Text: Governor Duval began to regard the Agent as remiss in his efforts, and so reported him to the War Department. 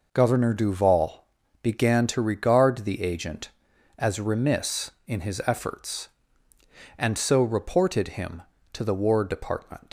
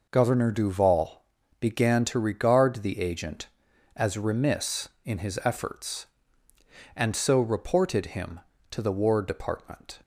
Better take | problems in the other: second | pauses between "Duval" and "began"; at 1.2 s; 0.38 s long; also in the second // leaves "Department" unfinished; at 9.8 s; 115 ms

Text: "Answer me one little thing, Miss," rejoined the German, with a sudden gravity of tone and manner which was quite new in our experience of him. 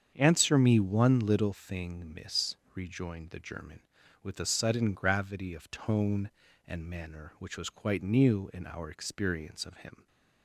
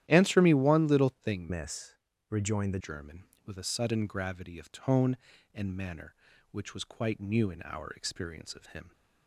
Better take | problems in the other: first | starts louder than the rest; strong; until 1.0 s; 12 dB; strong in the first // changes voice from "Miss" to "the"; from 1.4 to 2.7 s; 1.3 s long

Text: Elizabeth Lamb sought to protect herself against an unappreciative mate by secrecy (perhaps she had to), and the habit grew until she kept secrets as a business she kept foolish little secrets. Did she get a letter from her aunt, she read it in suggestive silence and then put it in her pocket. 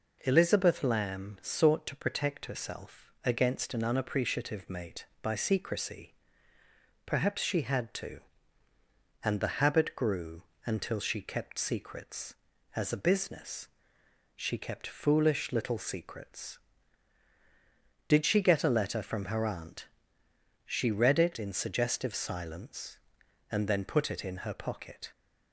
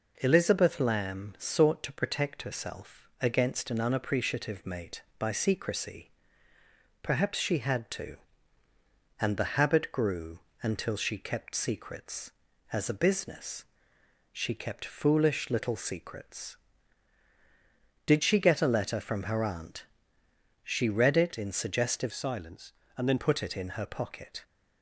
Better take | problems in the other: first | pauses between "grew" and "until"; slight; at 10.3 s; 0.24 s long; slight in the first // pauses between "business" and "she"; noticeable; at 13.6 s; 0.68 s long; noticeable in the first // changes voice from "silence" to "then"; from 22.1 to 23.1 s; 1.0 s long

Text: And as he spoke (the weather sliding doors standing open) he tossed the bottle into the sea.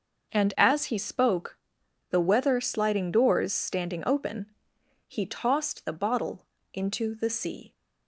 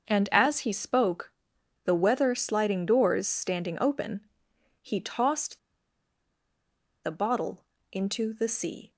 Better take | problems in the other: first | starts louder than the rest; until 1.1 s; 6 dB; noticeable in the first // pauses between "tossed" and "the"; strong; at 5.5 s; 1.4 s long // pauses between "bottle" and "into"; slight; at 7.6 s; 0.26 s long; slight in the first

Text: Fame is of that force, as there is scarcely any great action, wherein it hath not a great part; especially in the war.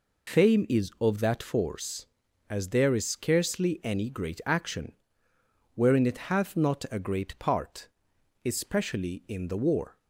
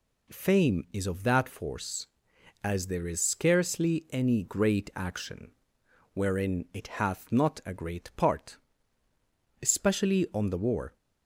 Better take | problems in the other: first | says "on" for "in"; at 10.3 s

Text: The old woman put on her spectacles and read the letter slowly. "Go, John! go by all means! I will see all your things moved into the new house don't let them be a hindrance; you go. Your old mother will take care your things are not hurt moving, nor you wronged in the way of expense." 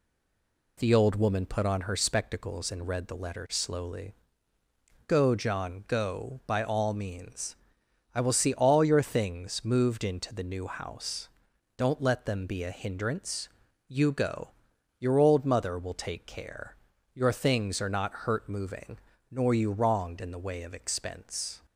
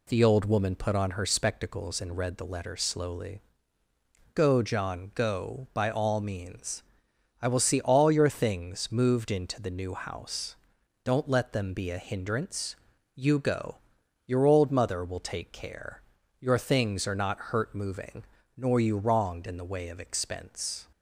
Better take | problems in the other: second | stays silent before the first word; slight; until 0.7 s; 0.7 s long // pauses between "house" and "don't"; noticeable; at 11.2 s; 0.48 s long; noticeable in the second // pauses between "care" and "your"; at 16.7 s; 0.38 s long; also in the second

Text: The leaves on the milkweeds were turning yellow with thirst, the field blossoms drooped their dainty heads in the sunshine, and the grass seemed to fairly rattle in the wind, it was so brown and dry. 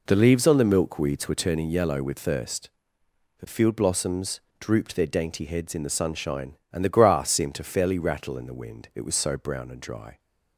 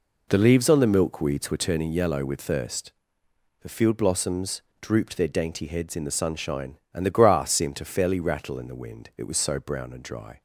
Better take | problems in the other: neither | pauses between "blossoms" and "drooped"; slight; the same in both

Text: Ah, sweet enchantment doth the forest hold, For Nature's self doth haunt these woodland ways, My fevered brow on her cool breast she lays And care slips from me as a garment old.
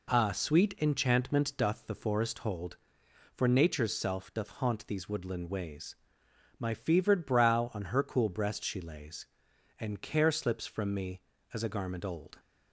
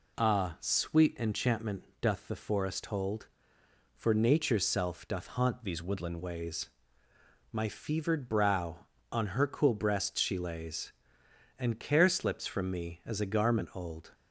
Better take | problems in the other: first | pauses between "enchantment" and "doth"; slight; at 1.8 s; 0.16 s long // changes voice from "these" to "woodland"; from 5.6 to 6.1 s; 0.5 s long

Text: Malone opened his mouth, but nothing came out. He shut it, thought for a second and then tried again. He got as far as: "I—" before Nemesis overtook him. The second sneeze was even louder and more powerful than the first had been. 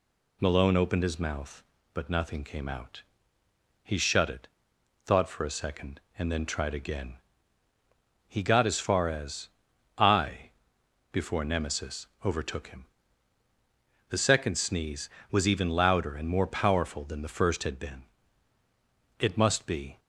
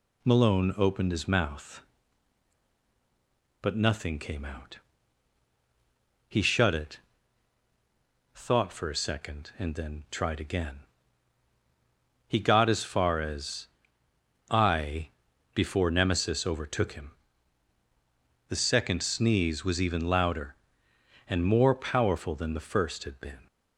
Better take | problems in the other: second | pauses between "Nemesis" and "overtook"; slight; at 12.0 s; 0.18 s long // goes on to say "It must be"; noticeable; from 19.2 s on; 0.78 s long

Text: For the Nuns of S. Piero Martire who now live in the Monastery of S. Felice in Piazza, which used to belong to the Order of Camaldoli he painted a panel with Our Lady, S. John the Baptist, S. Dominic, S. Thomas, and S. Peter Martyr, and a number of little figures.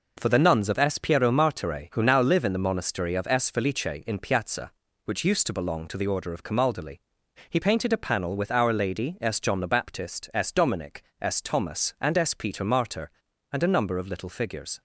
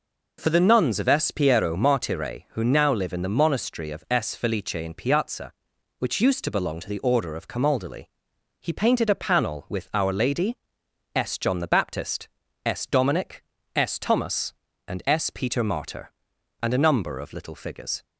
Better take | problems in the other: neither | pauses between "Camaldoli" and "he"; noticeable; the same in both

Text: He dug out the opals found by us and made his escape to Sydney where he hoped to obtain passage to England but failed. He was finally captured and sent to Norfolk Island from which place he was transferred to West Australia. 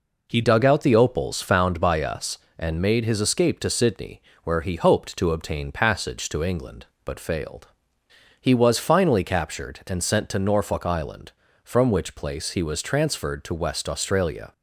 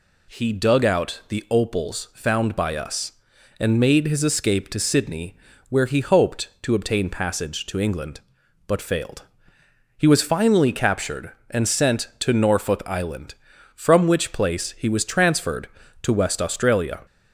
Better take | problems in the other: second | changes voice at "dug"; from 0.4 s on; 14.1 s long // pauses between "Sydney" and "where"; slight; at 4.2 s; 0.24 s long; slight in the second

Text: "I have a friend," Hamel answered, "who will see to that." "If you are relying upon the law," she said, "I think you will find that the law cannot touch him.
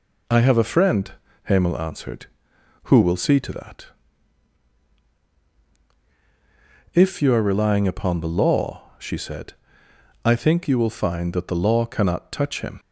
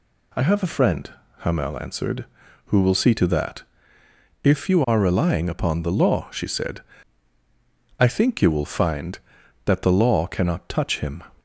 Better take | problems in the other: neither | none

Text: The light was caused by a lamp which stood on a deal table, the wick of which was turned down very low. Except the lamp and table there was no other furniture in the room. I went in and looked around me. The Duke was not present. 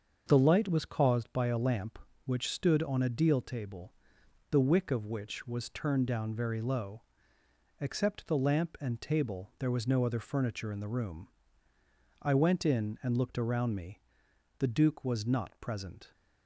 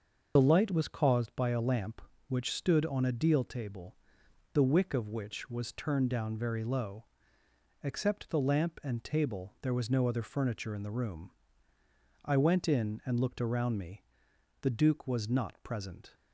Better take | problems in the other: first | loses the start of "The"; at 0.3 s; 50 ms // starts louder than the rest; until 1.3 s; 6 dB; also in the first

